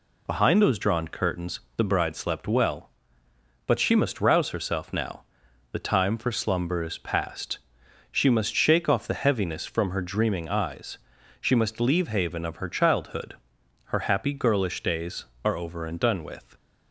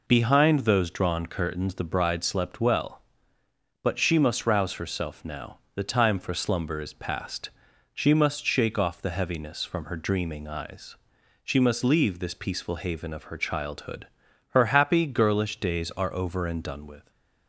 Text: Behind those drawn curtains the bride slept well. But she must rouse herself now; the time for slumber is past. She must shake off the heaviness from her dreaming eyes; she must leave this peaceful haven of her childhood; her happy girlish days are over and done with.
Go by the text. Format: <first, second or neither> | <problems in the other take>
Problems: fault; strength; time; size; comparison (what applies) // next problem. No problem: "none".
second | pauses between "curtains" and "the"; slight; at 1.5 s; 0.18 s long // skips "this peaceful"; at 12.0 s